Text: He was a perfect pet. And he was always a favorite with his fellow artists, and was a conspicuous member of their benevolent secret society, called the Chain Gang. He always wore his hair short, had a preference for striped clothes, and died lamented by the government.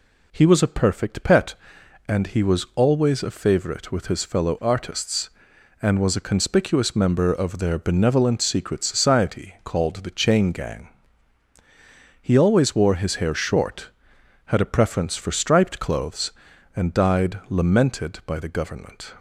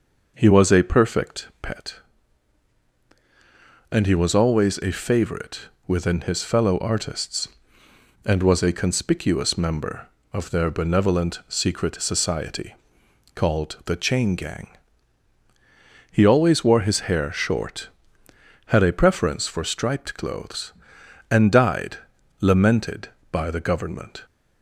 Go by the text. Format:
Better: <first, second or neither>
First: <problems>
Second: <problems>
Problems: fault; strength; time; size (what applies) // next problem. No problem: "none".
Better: first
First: none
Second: says "within" for "with"; at 5.8 s // pauses between "died" and "lamented"; at 21.9 s; 0.44 s long